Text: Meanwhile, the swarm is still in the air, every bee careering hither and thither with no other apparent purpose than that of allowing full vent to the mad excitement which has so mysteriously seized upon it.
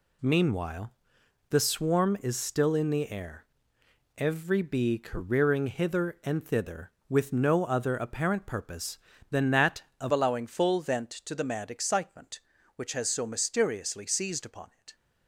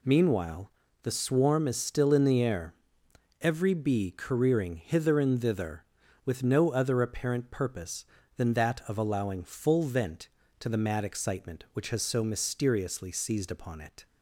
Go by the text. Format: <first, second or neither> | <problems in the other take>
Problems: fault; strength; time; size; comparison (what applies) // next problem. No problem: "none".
second | changes voice at "allowing"; from 10.1 s on; 4.8 s long